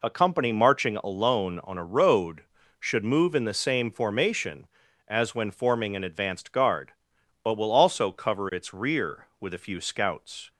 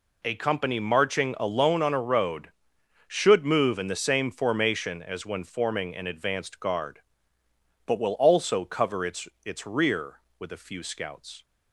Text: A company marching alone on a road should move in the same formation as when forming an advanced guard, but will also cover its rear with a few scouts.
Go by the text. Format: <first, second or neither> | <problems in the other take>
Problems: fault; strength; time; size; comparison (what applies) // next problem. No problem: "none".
first | says "its" twice; at 9.4 s